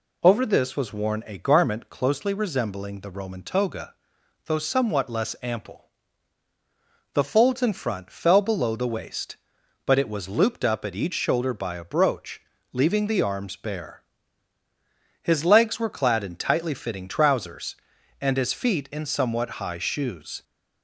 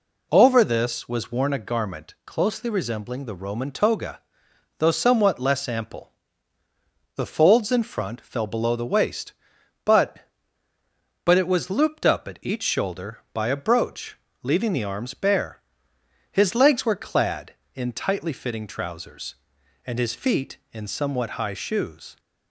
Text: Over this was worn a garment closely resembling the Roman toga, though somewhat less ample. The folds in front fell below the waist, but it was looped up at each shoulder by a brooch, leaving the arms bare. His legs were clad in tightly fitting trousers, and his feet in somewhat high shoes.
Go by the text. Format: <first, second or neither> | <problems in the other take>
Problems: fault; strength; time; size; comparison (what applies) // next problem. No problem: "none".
first | says "but" twice; at 11.2 s